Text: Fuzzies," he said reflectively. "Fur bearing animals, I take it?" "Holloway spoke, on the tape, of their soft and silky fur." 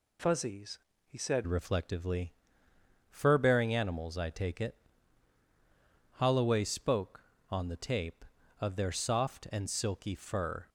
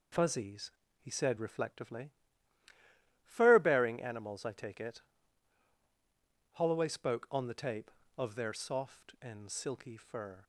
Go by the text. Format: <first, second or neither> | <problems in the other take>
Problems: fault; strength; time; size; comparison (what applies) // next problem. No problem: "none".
second | changes voice at "reflectively"; from 1.4 s on; 9.2 s long